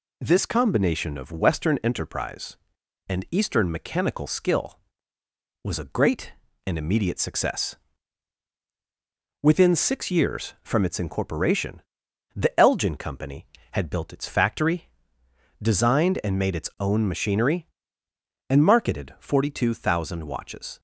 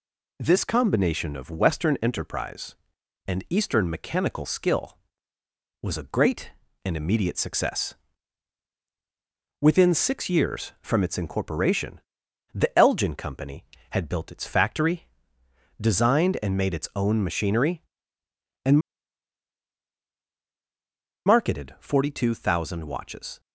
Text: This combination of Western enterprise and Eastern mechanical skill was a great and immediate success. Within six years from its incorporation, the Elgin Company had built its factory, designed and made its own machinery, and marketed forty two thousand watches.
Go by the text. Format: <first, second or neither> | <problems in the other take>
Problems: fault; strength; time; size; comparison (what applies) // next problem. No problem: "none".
first | pauses between "and" and "marketed"; strong; at 18.7 s; 2.4 s long